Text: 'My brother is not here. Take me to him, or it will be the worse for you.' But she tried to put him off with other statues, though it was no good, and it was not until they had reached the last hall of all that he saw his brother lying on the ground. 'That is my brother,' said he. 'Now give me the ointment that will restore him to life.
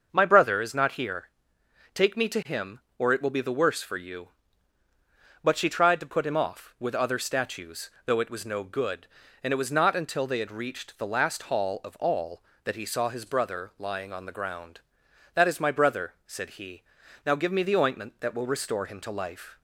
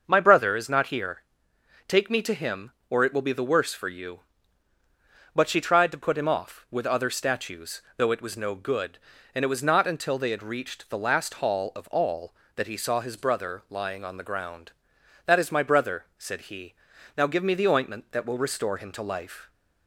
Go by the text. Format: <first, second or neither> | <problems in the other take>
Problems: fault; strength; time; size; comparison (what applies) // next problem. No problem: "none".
neither | starts louder than the rest; the same in both